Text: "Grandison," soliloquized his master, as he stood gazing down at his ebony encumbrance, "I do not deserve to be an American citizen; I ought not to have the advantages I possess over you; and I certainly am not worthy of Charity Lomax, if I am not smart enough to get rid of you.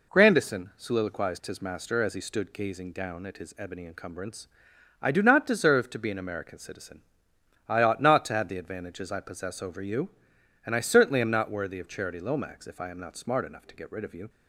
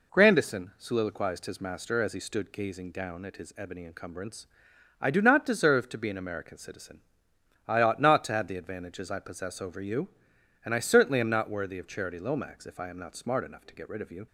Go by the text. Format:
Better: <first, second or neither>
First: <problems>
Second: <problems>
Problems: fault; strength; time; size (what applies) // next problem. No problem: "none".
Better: neither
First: none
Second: none